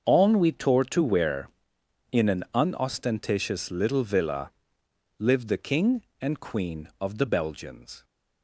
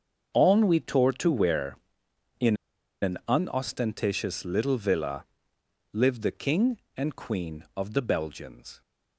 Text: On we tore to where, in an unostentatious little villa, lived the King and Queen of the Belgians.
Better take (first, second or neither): first